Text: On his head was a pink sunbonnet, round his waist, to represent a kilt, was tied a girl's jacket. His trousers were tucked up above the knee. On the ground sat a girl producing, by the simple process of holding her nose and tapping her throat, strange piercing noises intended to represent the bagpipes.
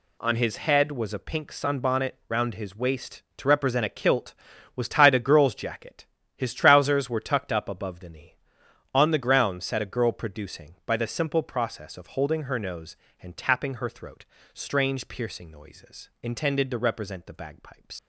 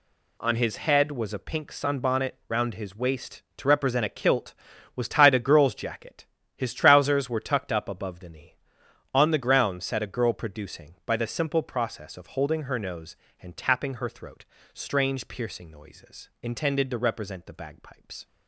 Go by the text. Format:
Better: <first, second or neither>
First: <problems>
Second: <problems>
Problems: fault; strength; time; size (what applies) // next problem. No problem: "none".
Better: second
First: leaves "bagpipes" unfinished; at 17.9 s; 75 ms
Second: none